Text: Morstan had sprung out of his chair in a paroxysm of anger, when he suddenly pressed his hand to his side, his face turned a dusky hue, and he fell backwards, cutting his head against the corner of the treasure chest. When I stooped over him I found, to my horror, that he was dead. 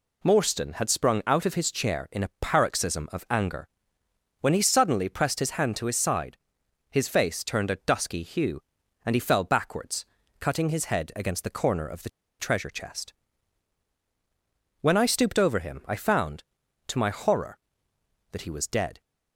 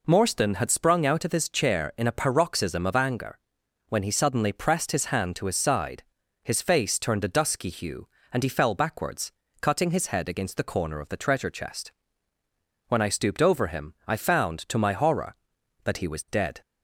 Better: second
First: pauses between "the" and "treasure"; slight; at 12.0 s; 0.29 s long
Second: none

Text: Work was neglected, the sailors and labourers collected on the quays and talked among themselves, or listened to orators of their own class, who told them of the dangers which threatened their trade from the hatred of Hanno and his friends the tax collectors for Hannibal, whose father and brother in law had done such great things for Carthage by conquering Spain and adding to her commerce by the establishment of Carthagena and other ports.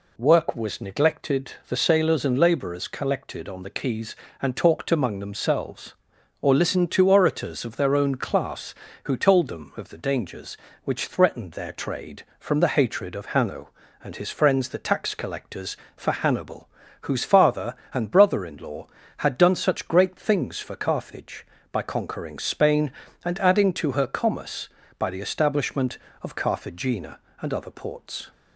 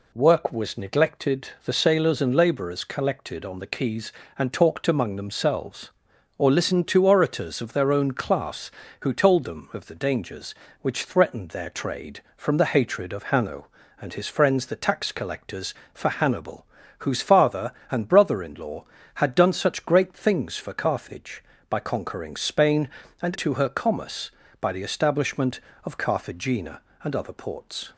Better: first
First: none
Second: skips "adding"; at 23.3 s

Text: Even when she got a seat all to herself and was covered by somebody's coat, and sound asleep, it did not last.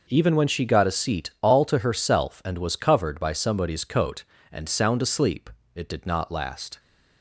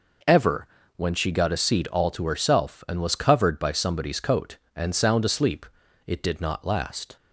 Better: first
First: none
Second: says "Ever" for "Even"; at 0.2 s

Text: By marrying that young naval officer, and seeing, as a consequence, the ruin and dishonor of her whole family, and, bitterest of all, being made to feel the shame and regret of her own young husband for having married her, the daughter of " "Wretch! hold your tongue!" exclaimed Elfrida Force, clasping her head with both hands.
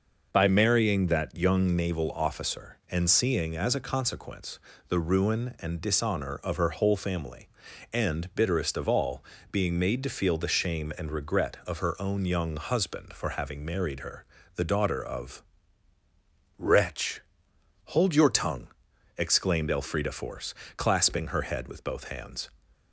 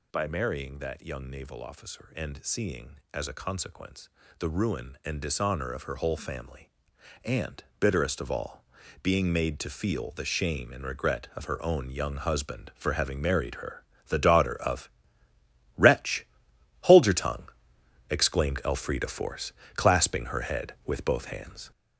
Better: first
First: none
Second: gets louder; noticeable; throughout; 5 dB

